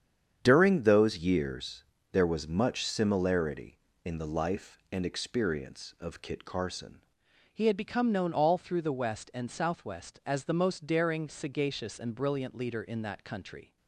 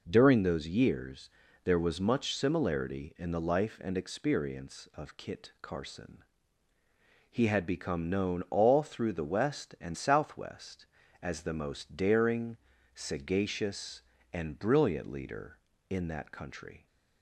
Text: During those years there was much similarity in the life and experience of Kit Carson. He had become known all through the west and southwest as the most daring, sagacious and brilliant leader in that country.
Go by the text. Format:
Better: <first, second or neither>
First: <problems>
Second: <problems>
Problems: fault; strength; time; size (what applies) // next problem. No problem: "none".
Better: second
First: starts louder than the rest; strong; until 1.4 s; 8 dB // pauses between "years" and "there"; slight; at 1.8 s; 0.28 s long // changes voice at "He"; from 7.5 s on; 6.2 s long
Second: pauses between "years" and "there"; slight; at 1.3 s; 0.34 s long